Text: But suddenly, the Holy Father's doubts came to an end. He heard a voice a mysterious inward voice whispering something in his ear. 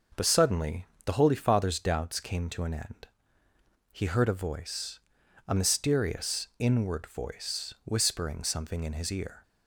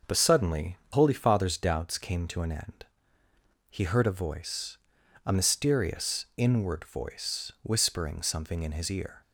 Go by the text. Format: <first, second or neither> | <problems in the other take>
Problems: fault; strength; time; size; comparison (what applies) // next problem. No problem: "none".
first | starts louder than the rest; noticeable; until 1.2 s; 6 dB // skips "the"; at 0.8 s // pauses between "voice" and "a"; noticeable; at 4.7 s; 0.46 s long; noticeable in the first